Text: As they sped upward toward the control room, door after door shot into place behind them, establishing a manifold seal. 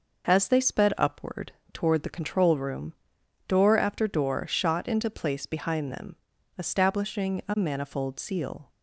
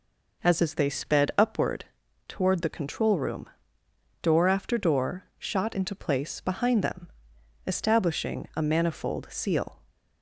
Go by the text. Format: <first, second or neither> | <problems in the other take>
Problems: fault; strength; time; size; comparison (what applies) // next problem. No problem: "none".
first | says "As" twice; at 0.6 s // pauses between "upward" and "toward"; at 1.8 s; 0.42 s long; slight in the first // pauses between "door" and "shot"; slight; at 5.2 s; 0.16 s long